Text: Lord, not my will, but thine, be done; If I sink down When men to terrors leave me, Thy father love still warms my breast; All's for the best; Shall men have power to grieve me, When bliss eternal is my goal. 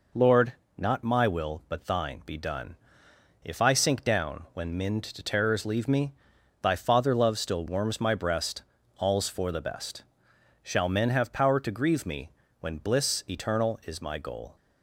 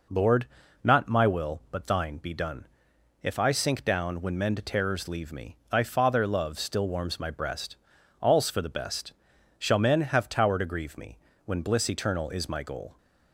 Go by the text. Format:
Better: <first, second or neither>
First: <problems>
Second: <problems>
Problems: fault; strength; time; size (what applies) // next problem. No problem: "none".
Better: first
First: none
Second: says "tower" for "power"; at 10.2 s